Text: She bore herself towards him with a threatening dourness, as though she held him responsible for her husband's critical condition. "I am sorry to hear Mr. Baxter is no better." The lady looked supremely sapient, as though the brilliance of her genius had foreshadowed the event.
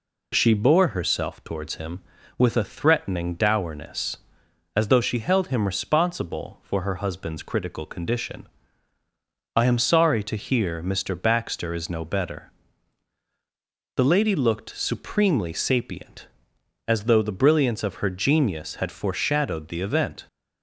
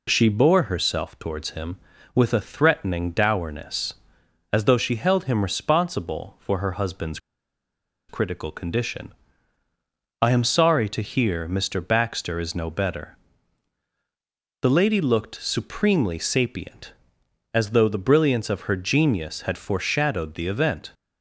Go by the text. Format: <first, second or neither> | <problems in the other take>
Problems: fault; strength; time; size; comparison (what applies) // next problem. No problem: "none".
first | pauses between "husband's" and "critical"; noticeable; at 7.1 s; 0.90 s long